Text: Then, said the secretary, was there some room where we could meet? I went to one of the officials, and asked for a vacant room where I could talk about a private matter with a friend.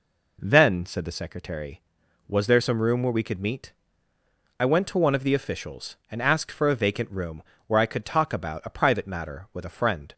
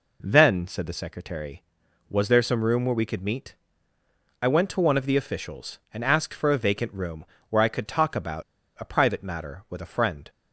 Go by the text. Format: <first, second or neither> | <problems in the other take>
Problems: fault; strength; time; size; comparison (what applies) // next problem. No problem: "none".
first | pauses between "room" and "where"; slight; at 7.2 s; 0.24 s long; slight in the first // pauses between "about" and "a"; at 8.4 s; 0.36 s long